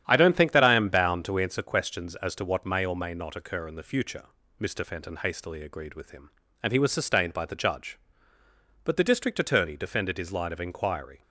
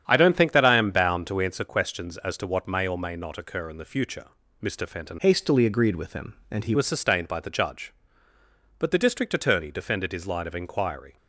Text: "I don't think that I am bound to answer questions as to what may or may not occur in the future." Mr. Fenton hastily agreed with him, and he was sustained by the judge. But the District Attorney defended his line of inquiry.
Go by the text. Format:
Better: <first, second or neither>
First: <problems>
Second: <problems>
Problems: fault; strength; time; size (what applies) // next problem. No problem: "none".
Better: first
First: starts louder than the rest; strong; until 1.0 s; 9.5 dB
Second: starts louder than the rest; strong; until 1.0 s; 9 dB // changes voice from "hastily" to "he"; from 5.1 to 6.7 s; 1.6 s long